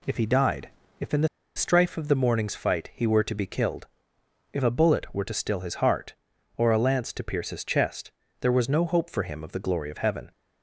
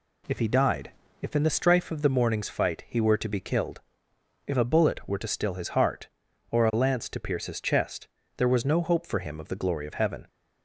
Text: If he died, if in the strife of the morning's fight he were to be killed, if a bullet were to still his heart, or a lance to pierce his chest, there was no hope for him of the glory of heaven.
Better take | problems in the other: second | pauses between "the" and "strife"; slight; at 1.2 s; 0.28 s long

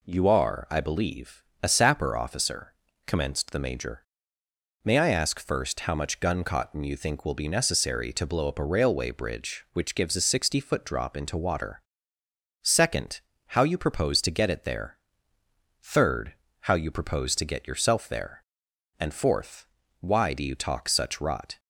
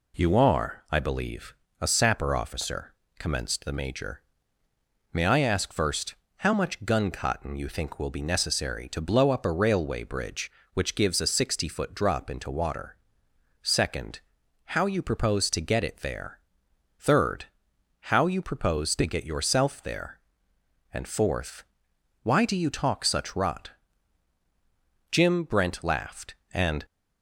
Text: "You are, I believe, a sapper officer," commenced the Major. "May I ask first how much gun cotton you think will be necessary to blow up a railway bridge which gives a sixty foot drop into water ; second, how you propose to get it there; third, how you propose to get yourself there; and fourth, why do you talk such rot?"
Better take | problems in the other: first | pauses between "first" and "how"; slight; at 6.1 s; 0.22 s long // goes on to say "Jim Brent laughed and"; strong; from 25.1 s on; 1.7 s long

